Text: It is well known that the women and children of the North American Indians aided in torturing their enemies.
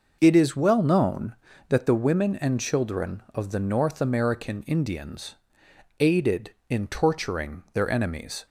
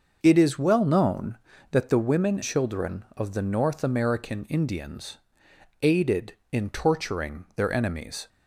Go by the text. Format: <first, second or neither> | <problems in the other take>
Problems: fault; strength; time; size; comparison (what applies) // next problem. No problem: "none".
first | starts louder than the rest; until 1.2 s; 6.5 dB // skips "and"; at 2.4 s // pauses between "Indians" and "aided"; noticeable; at 5.1 s; 0.64 s long; noticeable in the first